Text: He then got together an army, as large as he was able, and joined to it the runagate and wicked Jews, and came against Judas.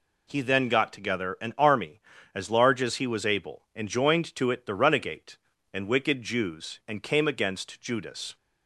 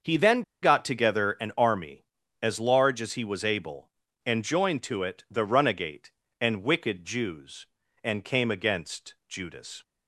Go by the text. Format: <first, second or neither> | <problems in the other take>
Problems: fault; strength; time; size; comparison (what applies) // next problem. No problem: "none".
first | starts louder than the rest; until 1.2 s; 6.5 dB // pauses between "then" and "got"; slight; at 0.4 s; 0.20 s long